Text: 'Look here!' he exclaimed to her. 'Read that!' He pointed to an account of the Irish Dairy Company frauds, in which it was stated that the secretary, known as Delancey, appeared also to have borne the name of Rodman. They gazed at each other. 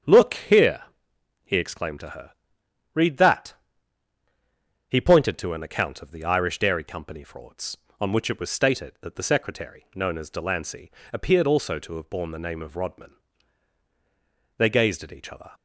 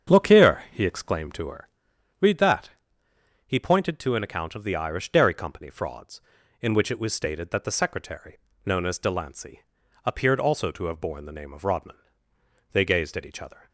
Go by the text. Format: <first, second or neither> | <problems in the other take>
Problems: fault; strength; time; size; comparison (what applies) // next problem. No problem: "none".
second | starts louder than the rest; strong; until 1.6 s; 8 dB; strong in the second // says "on" for "in"; at 8.0 s